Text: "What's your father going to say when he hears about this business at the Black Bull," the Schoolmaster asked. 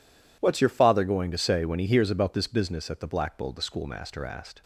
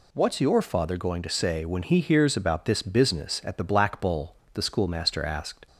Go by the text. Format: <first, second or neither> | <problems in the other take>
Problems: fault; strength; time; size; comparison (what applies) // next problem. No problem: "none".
neither | none